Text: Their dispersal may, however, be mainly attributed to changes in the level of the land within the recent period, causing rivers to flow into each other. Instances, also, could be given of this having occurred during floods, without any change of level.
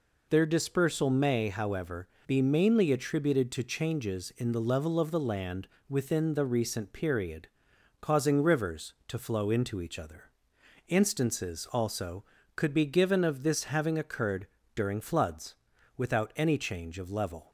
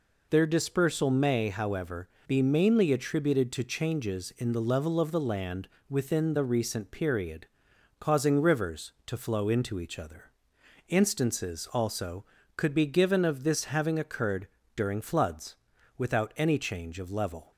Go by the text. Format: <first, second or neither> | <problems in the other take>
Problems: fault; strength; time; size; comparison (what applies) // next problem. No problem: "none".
neither | pauses between "land" and "within"; slight; the same in both // pauses between "occurred" and "during"; slight; the same in both